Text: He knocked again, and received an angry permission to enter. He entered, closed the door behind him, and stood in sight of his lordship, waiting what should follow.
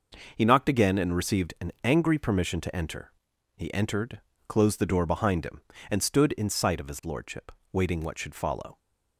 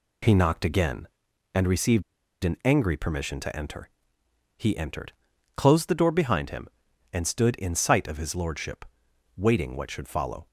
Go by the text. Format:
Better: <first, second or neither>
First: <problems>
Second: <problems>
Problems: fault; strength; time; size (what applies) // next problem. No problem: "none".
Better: first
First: none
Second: pauses between "received" and "an"; at 2.0 s; 0.41 s long